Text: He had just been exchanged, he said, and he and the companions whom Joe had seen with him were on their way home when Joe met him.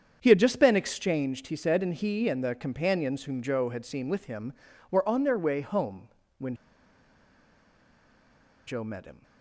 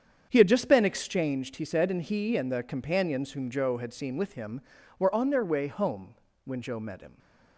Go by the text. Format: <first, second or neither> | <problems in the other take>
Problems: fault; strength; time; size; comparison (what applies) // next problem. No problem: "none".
second | starts louder than the rest; strong; until 1.2 s; 8 dB; strong in the second // pauses between "home" and "when"; slight; at 6.0 s; 0.30 s long; slight in the second // pauses between "when" and "Joe"; strong; at 6.5 s; 2.1 s long